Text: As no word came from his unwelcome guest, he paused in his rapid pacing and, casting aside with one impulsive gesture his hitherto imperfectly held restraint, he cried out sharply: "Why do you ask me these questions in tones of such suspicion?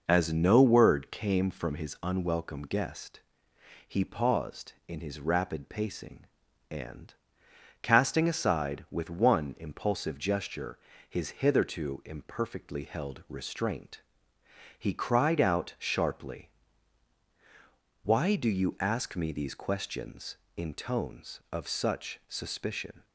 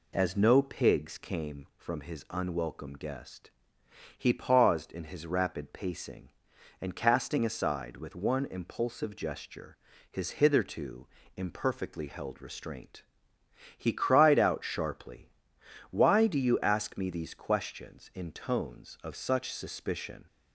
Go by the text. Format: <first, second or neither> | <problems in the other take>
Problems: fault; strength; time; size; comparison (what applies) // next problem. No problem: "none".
first | says "pigs" for "word"; at 0.6 s // pauses between "gesture" and "his"; slight; at 9.7 s; 0.32 s long; slight in the first // pauses between "hitherto" and "imperfectly"; slight; at 11.0 s; 0.28 s long